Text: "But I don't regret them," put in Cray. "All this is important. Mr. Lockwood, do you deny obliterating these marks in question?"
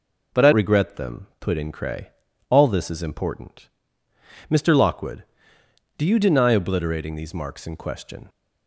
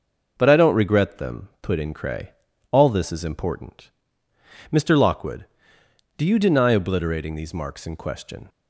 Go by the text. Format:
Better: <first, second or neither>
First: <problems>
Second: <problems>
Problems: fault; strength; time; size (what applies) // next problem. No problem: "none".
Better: second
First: skips "don't"; at 0.5 s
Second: none